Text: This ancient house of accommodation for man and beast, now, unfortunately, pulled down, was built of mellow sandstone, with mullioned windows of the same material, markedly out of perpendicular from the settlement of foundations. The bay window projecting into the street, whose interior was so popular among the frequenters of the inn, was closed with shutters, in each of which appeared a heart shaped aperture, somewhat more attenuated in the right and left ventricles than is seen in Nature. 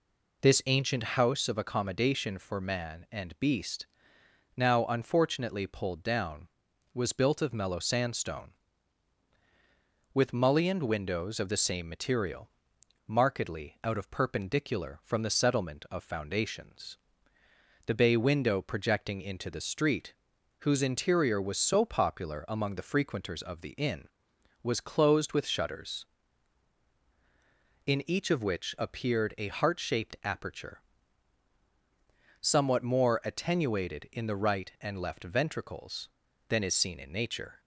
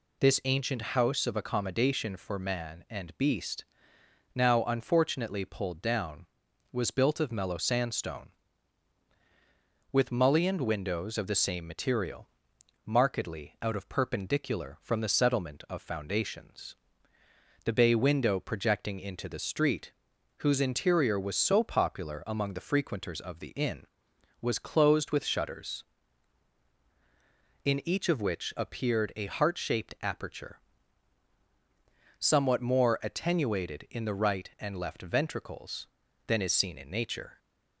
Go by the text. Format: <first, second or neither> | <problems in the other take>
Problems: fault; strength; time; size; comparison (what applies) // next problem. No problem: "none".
second | starts louder than the rest; until 1.3 s; 3.5 dB